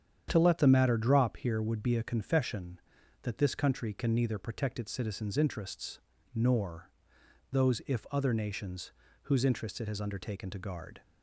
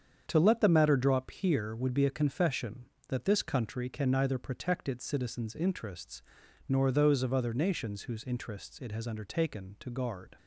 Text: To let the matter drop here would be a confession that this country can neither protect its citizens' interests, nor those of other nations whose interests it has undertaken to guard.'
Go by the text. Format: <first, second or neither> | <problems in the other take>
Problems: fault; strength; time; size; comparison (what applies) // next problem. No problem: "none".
second | starts louder than the rest; strong; until 1.3 s; 9 dB; strong in the second // pauses between "nor" and "those"; noticeable; at 6.9 s; 0.60 s long // says "if" for "of"; at 7.8 s // pauses between "nations" and "whose"; slight; at 8.9 s; 0.32 s long